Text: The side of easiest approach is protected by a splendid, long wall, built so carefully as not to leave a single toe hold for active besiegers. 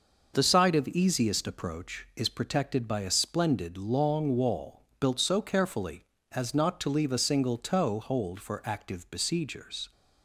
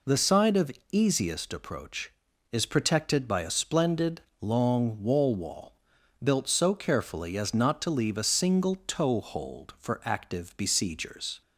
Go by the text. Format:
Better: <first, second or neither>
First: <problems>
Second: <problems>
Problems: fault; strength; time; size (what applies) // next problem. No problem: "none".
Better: first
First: none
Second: pauses between "of" and "easiest"; slight; at 0.7 s; 0.20 s long // says "wall" twice; at 5.3 s